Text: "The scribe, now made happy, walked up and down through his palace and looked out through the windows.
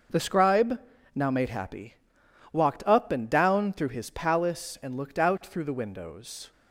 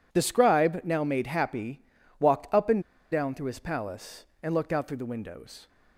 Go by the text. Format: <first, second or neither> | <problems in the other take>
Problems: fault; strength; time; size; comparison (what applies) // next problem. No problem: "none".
first | pauses between "and" and "down"; slight; at 2.8 s; 0.29 s long